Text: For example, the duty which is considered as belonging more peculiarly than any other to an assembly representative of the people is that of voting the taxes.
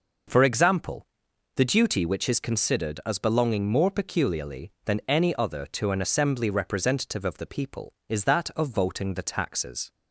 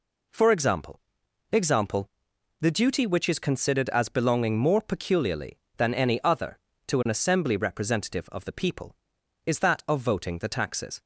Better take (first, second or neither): first